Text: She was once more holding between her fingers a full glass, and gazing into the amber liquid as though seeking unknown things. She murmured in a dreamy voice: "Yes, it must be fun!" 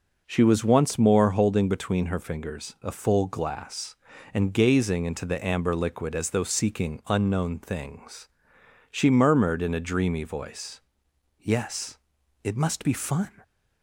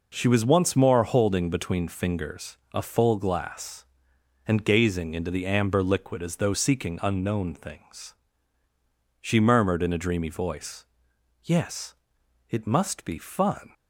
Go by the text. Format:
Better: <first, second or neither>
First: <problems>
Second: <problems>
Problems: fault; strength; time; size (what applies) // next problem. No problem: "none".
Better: first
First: none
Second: skips "her"; at 1.8 s